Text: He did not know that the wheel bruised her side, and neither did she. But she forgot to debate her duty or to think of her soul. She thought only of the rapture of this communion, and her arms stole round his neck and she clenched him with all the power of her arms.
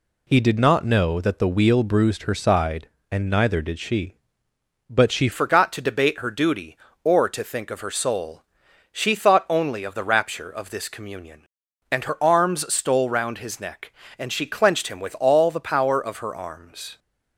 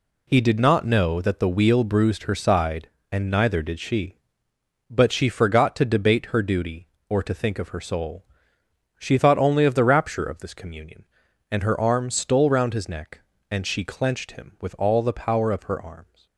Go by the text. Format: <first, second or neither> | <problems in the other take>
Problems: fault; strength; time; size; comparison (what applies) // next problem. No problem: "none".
second | changes voice at "forgot"; from 5.3 s on; 11.6 s long